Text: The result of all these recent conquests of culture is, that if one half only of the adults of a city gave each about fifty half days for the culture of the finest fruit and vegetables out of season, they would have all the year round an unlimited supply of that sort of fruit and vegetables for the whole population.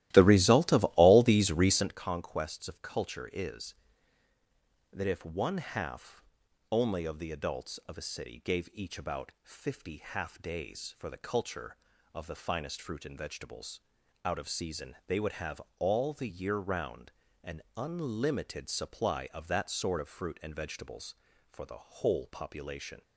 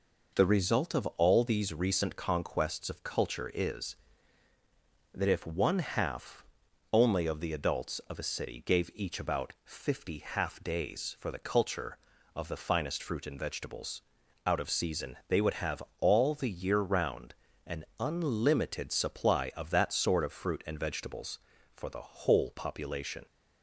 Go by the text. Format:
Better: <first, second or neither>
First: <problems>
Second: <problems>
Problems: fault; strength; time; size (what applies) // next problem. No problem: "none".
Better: second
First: starts louder than the rest; strong; until 2.0 s; 15.5 dB // pauses between "half" and "only"; noticeable; at 6.2 s; 0.52 s long // pauses between "vegetables" and "out"; noticeable; at 13.7 s; 0.46 s long // pauses between "have" and "all"; slight; at 15.6 s; 0.18 s long // pauses between "round" and "an"; slight; at 17.1 s; 0.32 s long // pauses between "an" and "unlimited"; slight; at 17.6 s; 0.16 s long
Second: pauses between "half" and "only"; noticeable; at 6.4 s; 0.52 s long // pauses between "vegetables" and "out"; noticeable; at 13.9 s; 0.46 s long // pauses between "have" and "all"; slight; at 15.8 s; 0.18 s long // pauses between "round" and "an"; slight; at 17.3 s; 0.32 s long // pauses between "an" and "unlimited"; slight; at 17.8 s; 0.16 s long